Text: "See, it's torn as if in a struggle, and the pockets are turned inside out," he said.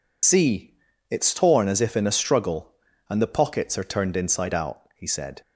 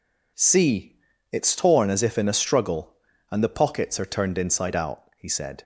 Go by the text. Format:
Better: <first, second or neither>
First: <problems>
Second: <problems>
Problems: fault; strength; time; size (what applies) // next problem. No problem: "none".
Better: second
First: loses the start of "See"; at 0.2 s; 90 ms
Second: none